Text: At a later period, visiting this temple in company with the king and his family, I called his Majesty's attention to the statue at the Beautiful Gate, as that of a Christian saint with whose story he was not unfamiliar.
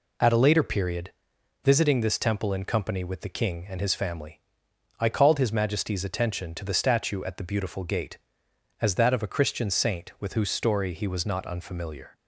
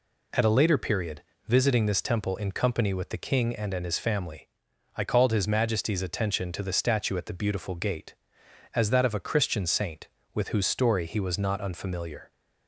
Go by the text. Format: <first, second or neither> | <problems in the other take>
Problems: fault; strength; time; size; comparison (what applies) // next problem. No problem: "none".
first | says "and" twice; at 3.7 s